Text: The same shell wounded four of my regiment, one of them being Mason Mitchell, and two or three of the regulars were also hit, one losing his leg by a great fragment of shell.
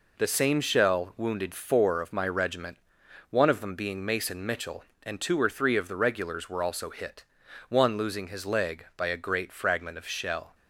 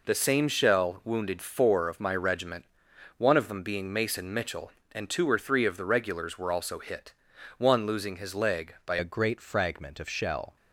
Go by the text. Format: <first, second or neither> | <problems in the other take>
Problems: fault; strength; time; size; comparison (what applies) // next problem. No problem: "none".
first | changes voice at "a"; from 8.9 s on; 1.6 s long